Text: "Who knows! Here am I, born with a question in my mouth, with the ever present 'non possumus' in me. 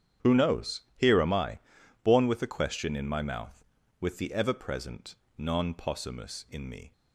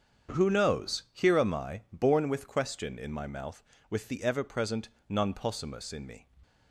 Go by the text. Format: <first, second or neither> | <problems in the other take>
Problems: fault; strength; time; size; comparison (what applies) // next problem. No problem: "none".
first | starts louder than the rest; strong; until 1.4 s; 7.5 dB; strong in the first // skips "a"; at 2.4 s // pauses between "present" and "non"; slight; at 4.8 s; 0.20 s long; slight in the first